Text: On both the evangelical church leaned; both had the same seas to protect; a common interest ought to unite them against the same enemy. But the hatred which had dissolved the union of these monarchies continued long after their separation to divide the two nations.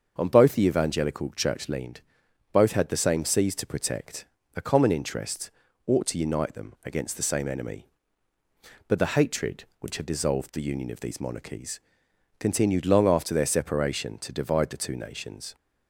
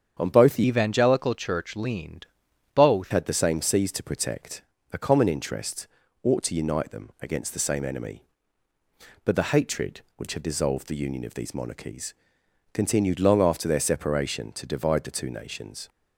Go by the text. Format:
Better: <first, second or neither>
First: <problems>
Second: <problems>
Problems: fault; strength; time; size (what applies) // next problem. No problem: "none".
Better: first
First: starts louder than the rest; until 1.1 s; 6.5 dB // pauses between "interest" and "ought"; slight; at 5.4 s; 0.36 s long // pauses between "monarchies" and "continued"; noticeable; at 11.7 s; 0.62 s long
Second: starts louder than the rest; strong; until 1.2 s; 7.5 dB // changes voice from "evangelical" to "both"; from 0.6 to 3.1 s; 2.5 s long // pauses between "interest" and "ought"; slight; at 5.8 s; 0.36 s long // pauses between "monarchies" and "continued"; noticeable; at 12.1 s; 0.62 s long